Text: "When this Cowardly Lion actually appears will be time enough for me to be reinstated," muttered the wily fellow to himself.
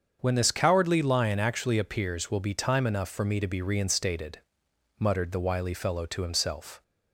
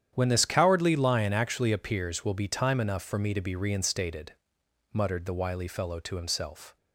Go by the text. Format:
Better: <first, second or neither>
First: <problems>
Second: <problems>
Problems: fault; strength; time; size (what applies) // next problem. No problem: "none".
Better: first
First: starts louder than the rest; strong; until 1.2 s; 7 dB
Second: gets quieter; strong; throughout; 13.5 dB // starts louder than the rest; strong; until 1.1 s; 9.5 dB